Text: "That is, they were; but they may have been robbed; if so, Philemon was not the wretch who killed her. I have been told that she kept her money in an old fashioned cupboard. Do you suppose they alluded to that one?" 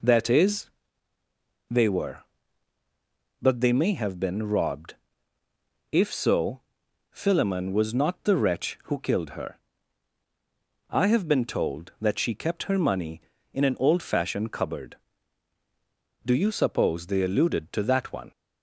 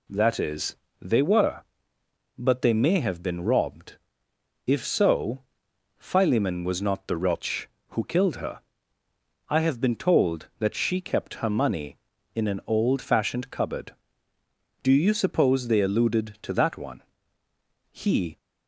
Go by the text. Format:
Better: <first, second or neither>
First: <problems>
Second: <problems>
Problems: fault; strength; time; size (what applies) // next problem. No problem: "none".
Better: first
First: none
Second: goes on to say "He"; slight; from 17.9 s on; 0.46 s long